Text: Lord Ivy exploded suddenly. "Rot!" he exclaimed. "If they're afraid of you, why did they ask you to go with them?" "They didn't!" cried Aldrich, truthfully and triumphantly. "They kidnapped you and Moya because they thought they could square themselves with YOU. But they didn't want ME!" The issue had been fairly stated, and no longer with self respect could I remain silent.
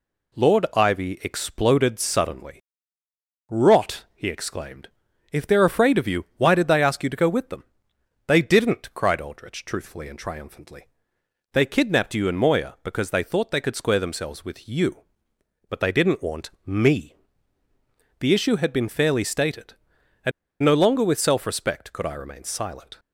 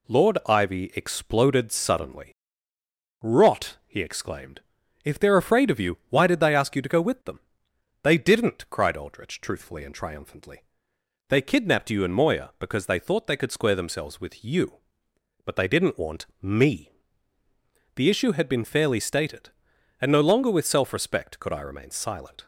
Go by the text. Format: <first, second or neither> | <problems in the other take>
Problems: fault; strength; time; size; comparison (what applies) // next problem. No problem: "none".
second | pauses between "want" and "ME"; slight; at 16.4 s; 0.16 s long; slight in the second // pauses between "and" and "no"; slight; at 20.3 s; 0.31 s long